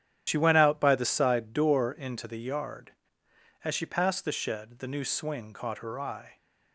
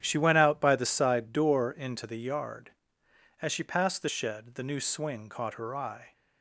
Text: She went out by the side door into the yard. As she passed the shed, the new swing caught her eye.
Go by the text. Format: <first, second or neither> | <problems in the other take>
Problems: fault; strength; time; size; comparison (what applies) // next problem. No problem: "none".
second | loses the start of "She"; at 0.2 s; 75 ms // starts louder than the rest; strong; until 1.2 s; 10.5 dB; strong in the second